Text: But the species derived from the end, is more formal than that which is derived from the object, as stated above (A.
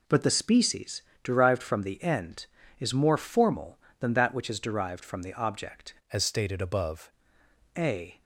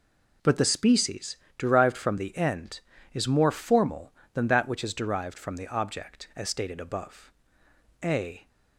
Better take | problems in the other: second | pauses between "species" and "derived"; slight; at 1.0 s; 0.22 s long; slight in the second // changes voice from "as" to "above"; from 6.1 to 7.1 s; 1.0 s long

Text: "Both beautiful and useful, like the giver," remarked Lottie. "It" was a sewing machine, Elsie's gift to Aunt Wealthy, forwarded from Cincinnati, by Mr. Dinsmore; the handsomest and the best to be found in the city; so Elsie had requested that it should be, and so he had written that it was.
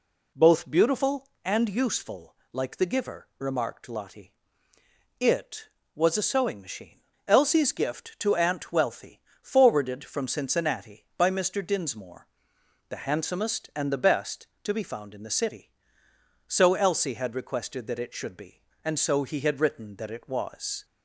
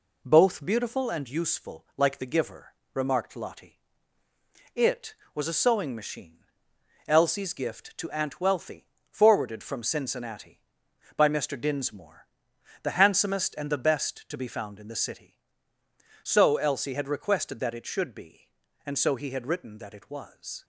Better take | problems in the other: first | gets quieter; throughout; 3.5 dB

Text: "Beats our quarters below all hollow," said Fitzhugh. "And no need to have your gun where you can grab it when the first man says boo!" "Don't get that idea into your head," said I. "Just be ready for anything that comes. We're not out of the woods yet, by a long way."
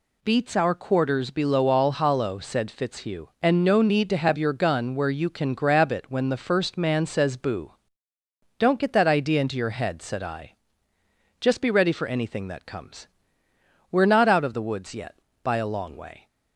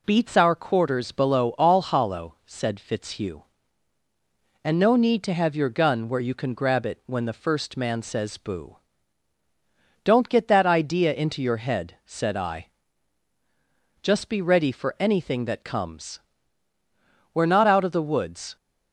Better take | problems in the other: first | stops before "yet by a long way"; at 18.5 s

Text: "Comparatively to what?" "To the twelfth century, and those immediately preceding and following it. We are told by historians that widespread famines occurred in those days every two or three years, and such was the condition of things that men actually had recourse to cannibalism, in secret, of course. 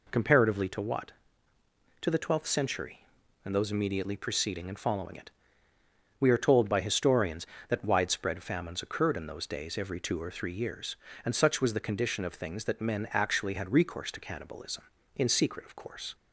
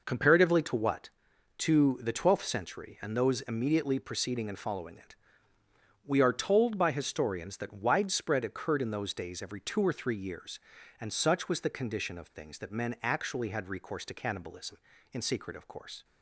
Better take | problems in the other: first | skips "famines"; at 8.4 s

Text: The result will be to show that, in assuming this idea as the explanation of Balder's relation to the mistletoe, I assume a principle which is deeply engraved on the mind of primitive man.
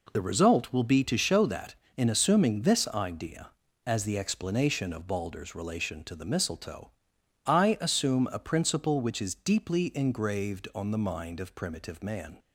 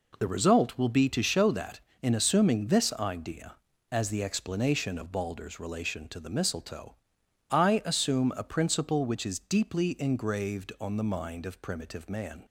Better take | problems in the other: neither | none

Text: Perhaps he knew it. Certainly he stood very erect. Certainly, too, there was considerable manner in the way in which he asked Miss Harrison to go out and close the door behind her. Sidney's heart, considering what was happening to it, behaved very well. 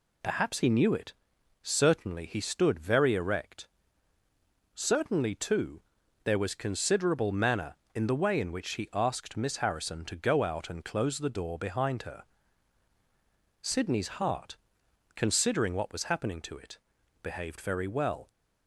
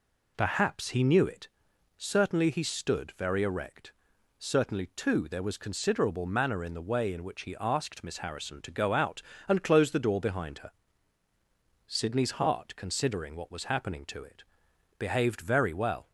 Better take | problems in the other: neither | none

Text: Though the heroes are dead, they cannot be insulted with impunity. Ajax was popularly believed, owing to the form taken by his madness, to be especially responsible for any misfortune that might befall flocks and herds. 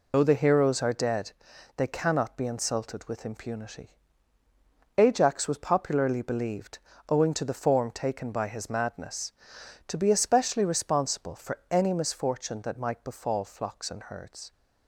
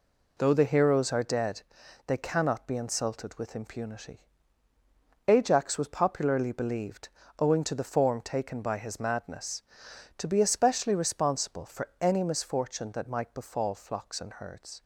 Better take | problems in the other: second | loses the start of "Though"; at 0.1 s; 65 ms

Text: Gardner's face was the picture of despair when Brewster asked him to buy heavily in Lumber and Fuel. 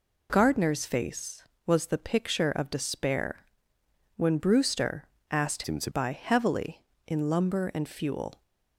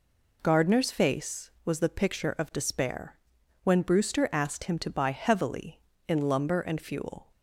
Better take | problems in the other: second | pauses between "despair" and "when"; noticeable; at 3.4 s; 0.68 s long; also in the second // pauses between "Brewster" and "asked"; slight; at 5.0 s; 0.20 s long // changes voice from "him" to "to"; from 5.6 to 5.9 s; 0.3 s long

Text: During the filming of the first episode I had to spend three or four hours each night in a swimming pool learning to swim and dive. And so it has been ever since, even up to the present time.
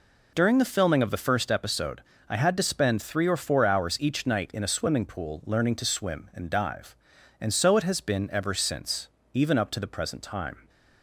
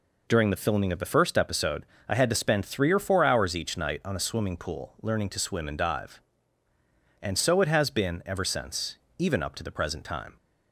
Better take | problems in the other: first | pauses between "episode" and "I"; slight; at 1.8 s; 0.24 s long; slight in the first // says "on" for "in"; at 4.0 s

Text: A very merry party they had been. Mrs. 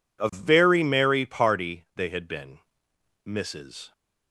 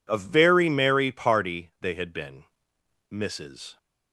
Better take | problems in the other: neither | none

